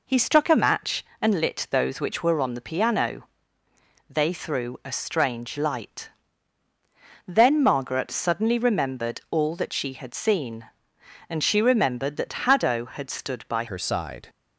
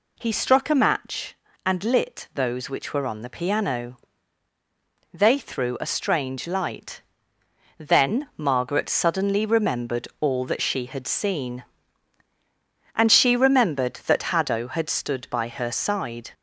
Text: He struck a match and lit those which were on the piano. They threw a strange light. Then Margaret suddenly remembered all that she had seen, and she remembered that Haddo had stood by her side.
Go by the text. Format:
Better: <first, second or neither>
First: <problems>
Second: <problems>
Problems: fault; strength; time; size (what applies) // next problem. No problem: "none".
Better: second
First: changes voice at "her"; from 13.6 s on; 0.6 s long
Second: none